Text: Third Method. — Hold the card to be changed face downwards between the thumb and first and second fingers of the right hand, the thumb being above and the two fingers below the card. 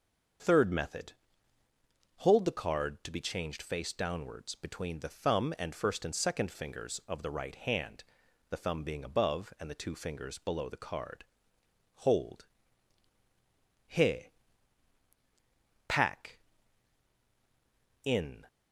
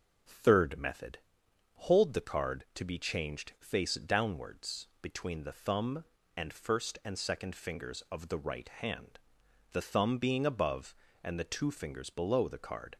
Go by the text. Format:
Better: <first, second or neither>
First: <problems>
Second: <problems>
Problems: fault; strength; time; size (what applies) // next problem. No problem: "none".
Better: second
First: starts louder than the rest; until 2.4 s; 6.5 dB // goes on to say "Hold he pack in"; strong; from 11.9 s on; 6.5 s long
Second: none